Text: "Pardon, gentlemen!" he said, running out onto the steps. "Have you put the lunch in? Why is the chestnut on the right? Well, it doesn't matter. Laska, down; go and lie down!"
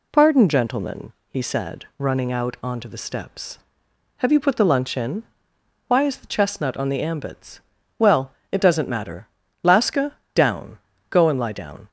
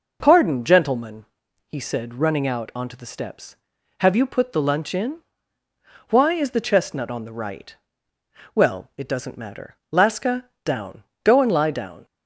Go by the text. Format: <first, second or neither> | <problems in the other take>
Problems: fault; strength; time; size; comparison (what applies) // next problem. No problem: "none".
second | says "ambits" for "right"; at 7.0 s